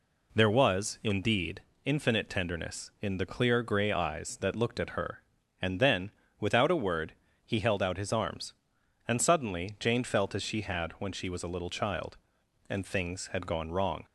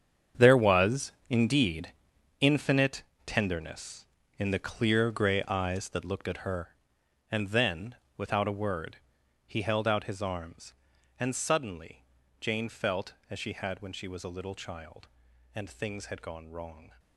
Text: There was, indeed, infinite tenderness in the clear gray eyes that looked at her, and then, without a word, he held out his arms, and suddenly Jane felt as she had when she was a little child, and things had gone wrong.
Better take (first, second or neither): first